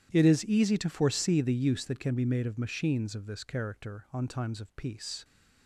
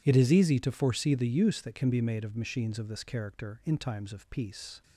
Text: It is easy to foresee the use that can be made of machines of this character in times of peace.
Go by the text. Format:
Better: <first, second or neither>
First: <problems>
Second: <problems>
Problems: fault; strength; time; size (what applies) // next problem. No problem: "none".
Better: second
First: starts louder than the rest; strong; until 1.1 s; 11 dB // says "on" for "in"; at 4.1 s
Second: none